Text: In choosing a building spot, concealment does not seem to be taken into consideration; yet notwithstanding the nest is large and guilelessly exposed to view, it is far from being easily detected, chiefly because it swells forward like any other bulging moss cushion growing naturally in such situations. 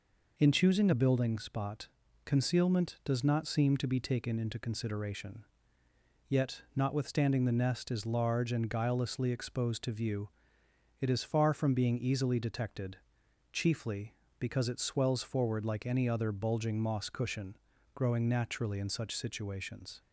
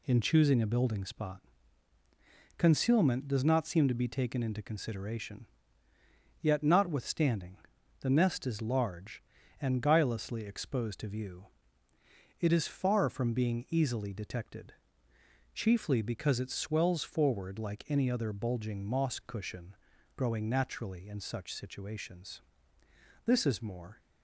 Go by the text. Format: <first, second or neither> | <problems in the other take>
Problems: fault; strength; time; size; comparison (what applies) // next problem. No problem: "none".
first | pauses between "notwithstanding" and "the"; noticeable; at 7.5 s; 0.46 s long // pauses between "cushion" and "growing"; at 19.7 s; 0.40 s long; slight in the first // goes on to say "This is more"; noticeable; from 23.2 s on; 0.74 s long